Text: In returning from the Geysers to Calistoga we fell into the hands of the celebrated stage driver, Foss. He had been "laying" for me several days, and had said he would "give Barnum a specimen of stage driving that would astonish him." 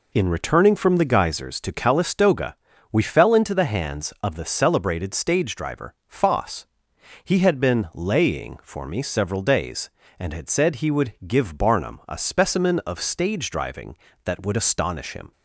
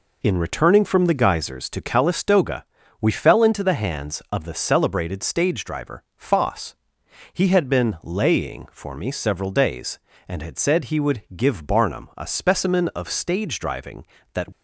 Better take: first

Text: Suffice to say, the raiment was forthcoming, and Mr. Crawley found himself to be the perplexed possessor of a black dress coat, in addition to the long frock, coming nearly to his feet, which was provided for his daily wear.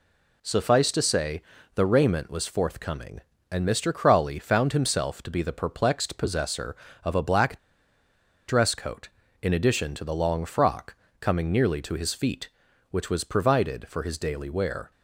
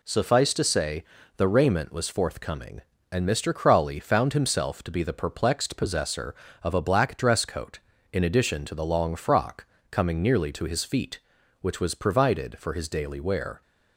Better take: second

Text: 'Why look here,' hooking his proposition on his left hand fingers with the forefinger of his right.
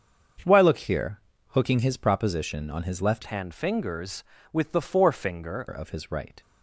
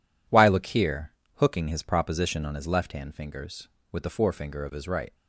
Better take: second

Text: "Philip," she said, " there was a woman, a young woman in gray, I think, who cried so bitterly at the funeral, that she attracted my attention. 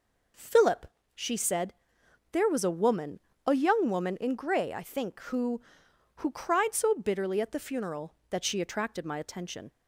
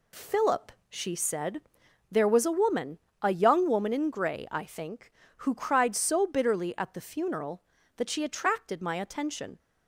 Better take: second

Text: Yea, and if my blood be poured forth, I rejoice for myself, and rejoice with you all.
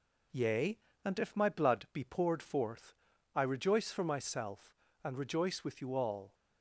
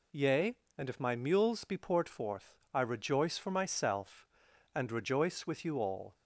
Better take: first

